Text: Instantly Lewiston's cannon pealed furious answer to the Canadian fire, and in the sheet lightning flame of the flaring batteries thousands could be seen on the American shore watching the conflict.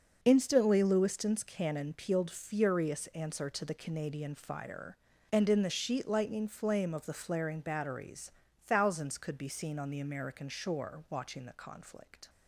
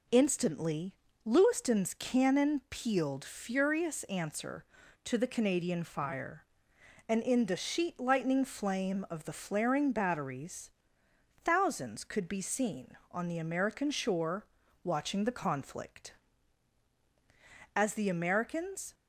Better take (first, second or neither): first